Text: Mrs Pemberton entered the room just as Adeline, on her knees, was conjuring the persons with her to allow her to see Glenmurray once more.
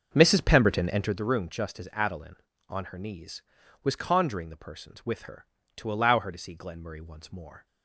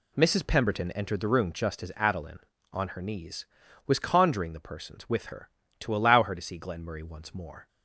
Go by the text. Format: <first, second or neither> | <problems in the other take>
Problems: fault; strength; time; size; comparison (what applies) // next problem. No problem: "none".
second | starts louder than the rest; until 1.2 s; 6.5 dB